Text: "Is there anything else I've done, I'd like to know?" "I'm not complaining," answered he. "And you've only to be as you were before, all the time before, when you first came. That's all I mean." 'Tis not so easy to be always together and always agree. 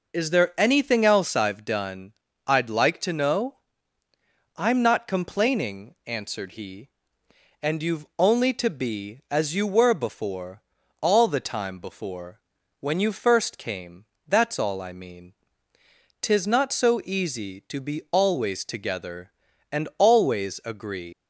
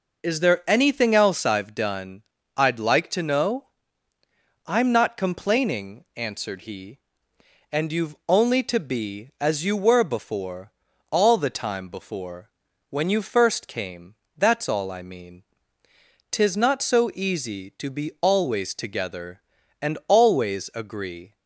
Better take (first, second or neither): second